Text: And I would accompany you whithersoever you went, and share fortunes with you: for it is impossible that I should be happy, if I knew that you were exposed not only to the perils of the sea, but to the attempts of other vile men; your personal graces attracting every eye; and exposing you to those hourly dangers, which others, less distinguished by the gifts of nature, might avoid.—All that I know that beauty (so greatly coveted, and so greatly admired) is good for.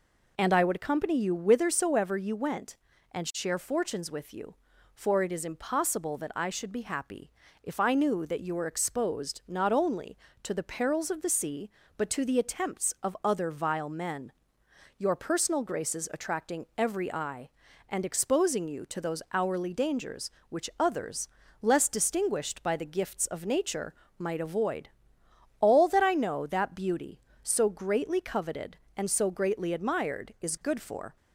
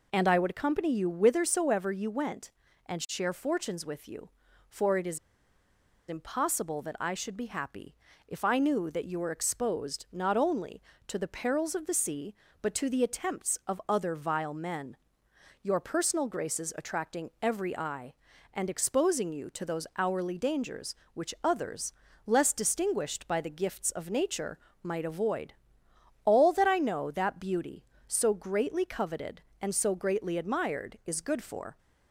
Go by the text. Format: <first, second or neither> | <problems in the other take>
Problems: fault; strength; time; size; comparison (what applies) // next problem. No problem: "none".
first | pauses between "is" and "impossible"; noticeable; at 5.1 s; 0.91 s long